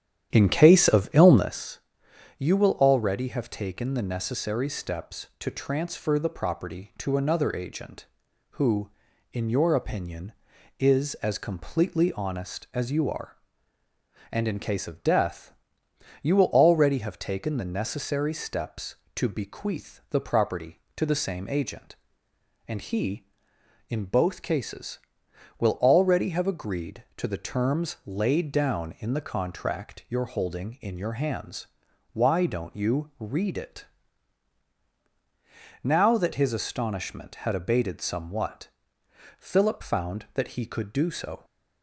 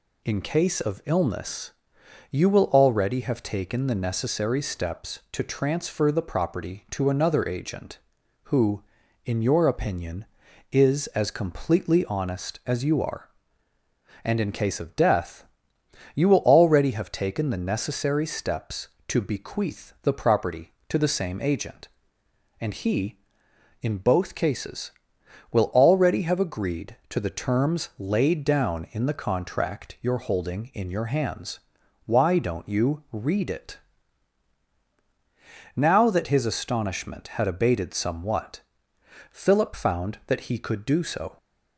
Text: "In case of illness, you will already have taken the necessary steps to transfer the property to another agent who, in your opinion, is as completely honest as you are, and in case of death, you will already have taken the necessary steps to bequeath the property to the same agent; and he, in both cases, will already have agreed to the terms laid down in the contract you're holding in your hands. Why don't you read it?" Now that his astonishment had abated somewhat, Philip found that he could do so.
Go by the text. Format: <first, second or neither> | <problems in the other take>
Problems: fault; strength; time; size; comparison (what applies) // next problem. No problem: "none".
second | starts louder than the rest; strong; until 1.5 s; 10.5 dB